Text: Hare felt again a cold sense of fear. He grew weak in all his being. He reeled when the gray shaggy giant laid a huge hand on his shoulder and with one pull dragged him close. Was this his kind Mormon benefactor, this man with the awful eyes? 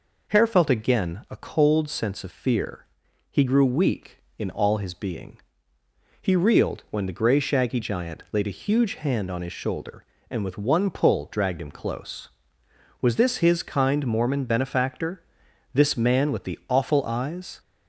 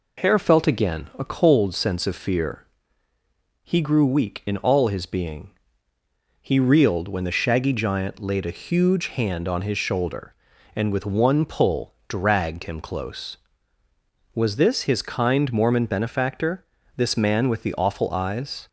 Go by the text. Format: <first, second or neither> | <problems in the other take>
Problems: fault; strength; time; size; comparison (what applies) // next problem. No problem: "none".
first | skips "gray"; at 7.2 s